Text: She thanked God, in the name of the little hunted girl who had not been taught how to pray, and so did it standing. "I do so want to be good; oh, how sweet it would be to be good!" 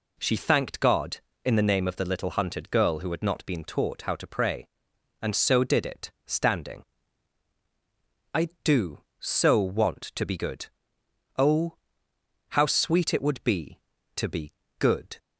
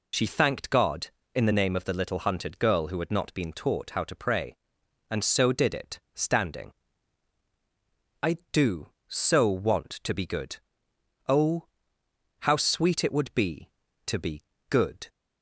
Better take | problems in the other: first | loses the start of "She"; at 0.1 s; 50 ms // pauses between "it" and "standing"; slight; at 5.9 s; 0.16 s long; slight in the first // pauses between "be" and "good"; slight; at 14.4 s; 0.24 s long; slight in the first

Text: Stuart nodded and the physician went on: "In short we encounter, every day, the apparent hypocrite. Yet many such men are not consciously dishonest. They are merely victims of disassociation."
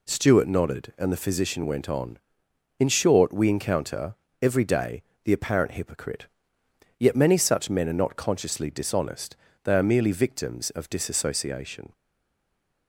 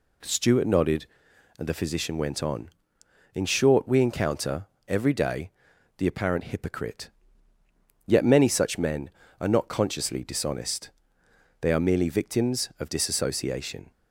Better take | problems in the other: second | stays silent after the last word; slight; from 11.9 s on; 0.9 s long

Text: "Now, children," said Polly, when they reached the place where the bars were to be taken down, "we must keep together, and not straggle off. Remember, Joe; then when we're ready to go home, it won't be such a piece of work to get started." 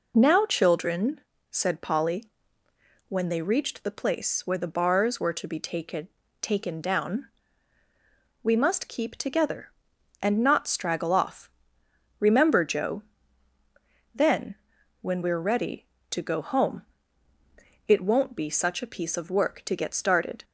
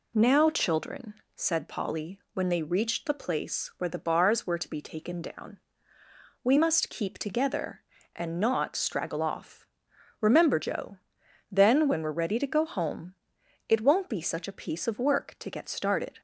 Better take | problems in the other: second | says "taken" twice; at 6.3 s // pauses between "then" and "when"; noticeable; at 14.5 s; 0.48 s long

